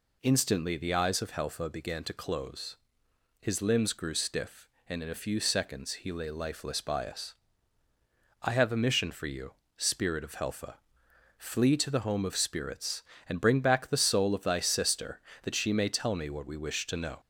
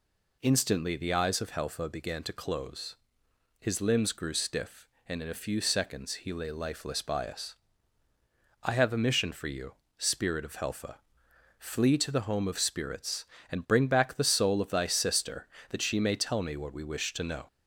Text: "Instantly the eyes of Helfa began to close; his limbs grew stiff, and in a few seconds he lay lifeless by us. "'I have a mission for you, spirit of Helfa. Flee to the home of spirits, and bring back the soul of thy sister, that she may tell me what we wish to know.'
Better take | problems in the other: neither | none

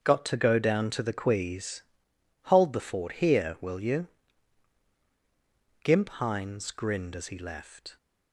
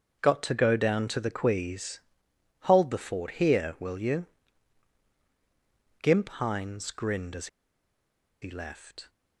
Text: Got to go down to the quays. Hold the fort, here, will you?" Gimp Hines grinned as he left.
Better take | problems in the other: first | starts louder than the rest; until 1.2 s; 6.5 dB; also in the first // pauses between "as" and "he"; noticeable; at 7.4 s; 0.95 s long

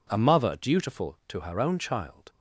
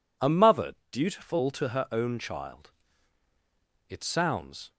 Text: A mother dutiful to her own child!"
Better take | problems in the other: first | pauses between "mother" and "dutiful"; slight; at 0.7 s; 0.16 s long // goes on to say "It sounds"; noticeable; from 3.8 s on; 0.84 s long

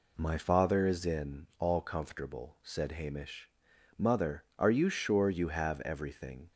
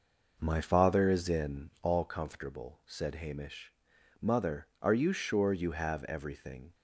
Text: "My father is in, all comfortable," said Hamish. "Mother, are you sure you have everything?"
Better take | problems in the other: first | starts louder than the rest; noticeable; until 2.1 s; 5.5 dB

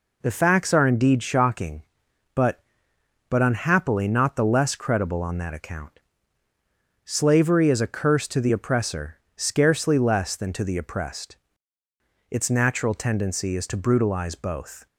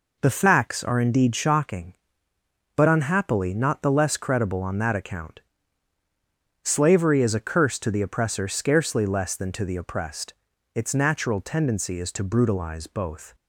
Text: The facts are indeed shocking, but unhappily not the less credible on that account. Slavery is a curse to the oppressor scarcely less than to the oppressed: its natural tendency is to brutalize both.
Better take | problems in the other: second | says "but" twice; at 3.3 s // pauses between "oppressor" and "scarcely"; slight; at 9.1 s; 0.22 s long

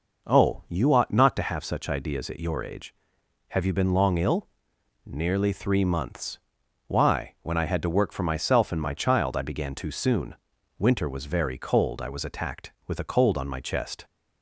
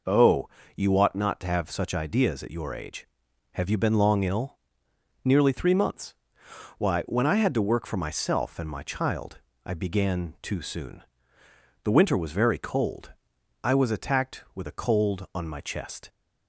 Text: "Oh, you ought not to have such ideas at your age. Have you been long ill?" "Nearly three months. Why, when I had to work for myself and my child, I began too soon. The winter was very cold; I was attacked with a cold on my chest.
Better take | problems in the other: second | skips "The"; at 10.5 s

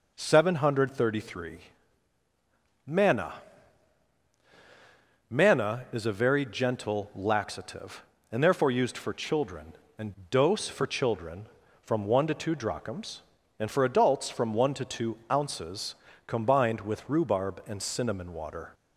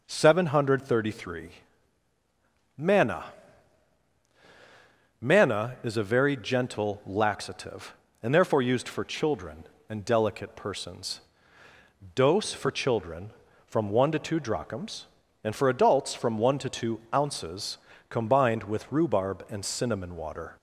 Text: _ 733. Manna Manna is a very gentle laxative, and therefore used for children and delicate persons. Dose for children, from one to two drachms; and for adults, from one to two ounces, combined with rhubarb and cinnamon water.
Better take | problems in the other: second | pauses between "Manna" and "Manna"; strong; at 3.3 s; 1.9 s long; strong in the second // skips "delicate persons"; at 10.2 s // pauses between "two" and "ounces"; slight; at 15.1 s; 0.16 s long; slight in the second

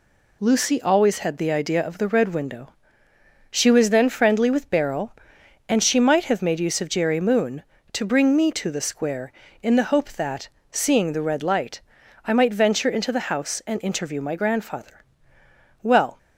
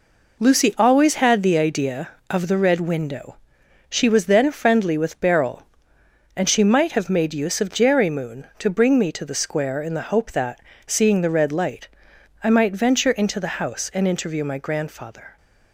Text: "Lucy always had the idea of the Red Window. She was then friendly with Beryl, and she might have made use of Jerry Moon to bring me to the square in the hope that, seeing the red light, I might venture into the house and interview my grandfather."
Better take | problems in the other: second | goes on to say "Well"; slight; from 15.8 s on; 0.36 s long

